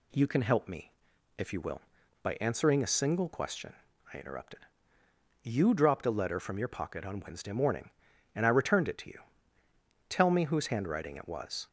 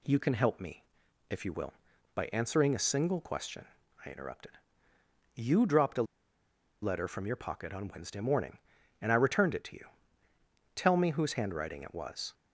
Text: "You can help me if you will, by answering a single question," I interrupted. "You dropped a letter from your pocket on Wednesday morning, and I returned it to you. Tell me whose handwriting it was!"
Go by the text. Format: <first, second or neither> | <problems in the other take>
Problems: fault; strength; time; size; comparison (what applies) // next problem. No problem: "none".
first | pauses between "me" and "if"; noticeable; at 0.8 s; 0.46 s long; noticeable in the first // pauses between "a" and "letter"; noticeable; at 6.0 s; 0.78 s long